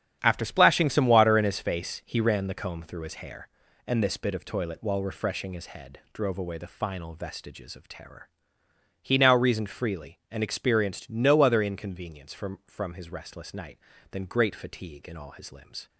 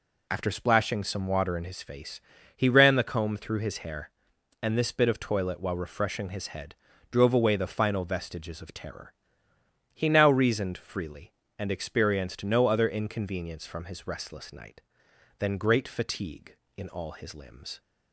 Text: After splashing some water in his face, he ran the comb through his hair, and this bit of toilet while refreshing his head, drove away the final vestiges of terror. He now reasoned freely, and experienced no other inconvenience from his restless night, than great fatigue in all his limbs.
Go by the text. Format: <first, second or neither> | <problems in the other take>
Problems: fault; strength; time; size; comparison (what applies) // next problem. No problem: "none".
second | starts louder than the rest; strong; until 1.2 s; 9 dB // says "from" twice; at 12.6 s